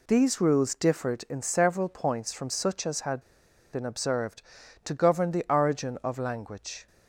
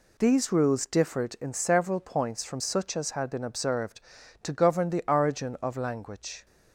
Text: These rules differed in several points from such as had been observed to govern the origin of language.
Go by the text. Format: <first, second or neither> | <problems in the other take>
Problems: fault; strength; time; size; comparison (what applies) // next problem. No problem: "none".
second | pauses between "had" and "been"; noticeable; at 3.2 s; 0.51 s long